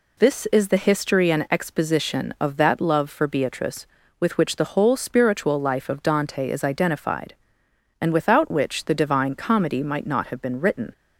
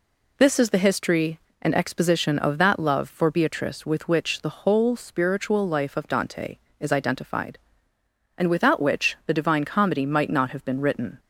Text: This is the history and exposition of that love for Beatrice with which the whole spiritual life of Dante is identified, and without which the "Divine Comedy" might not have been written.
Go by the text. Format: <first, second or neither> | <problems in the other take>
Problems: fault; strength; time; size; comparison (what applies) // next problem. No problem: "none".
neither | none